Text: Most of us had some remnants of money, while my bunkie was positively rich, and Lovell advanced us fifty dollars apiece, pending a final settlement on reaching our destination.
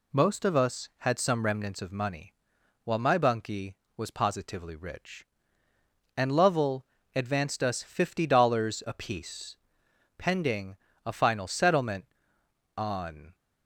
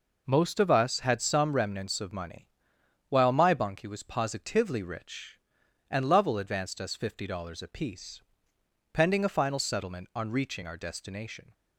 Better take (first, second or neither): second